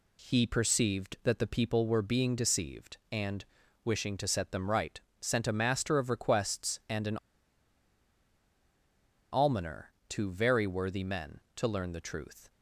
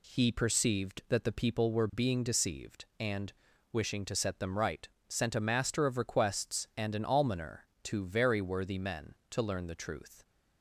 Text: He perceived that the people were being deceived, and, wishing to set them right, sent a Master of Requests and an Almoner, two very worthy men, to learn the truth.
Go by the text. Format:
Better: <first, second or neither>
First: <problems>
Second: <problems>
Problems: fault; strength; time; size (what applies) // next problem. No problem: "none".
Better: second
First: pauses between "an" and "Almoner"; strong; at 7.1 s; 2.1 s long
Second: none